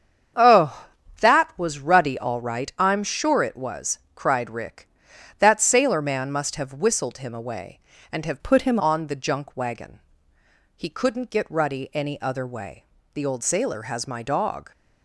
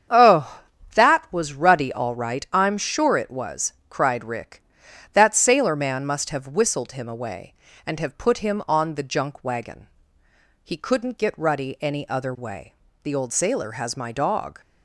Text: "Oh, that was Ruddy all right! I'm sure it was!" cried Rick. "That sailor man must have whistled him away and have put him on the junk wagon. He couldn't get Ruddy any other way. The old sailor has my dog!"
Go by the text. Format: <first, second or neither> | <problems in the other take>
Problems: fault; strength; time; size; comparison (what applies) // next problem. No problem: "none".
second | starts louder than the rest; strong; until 1.6 s; 7.5 dB; strong in the second // changes voice from "put" to "him"; from 8.4 to 8.7 s; 0.3 s long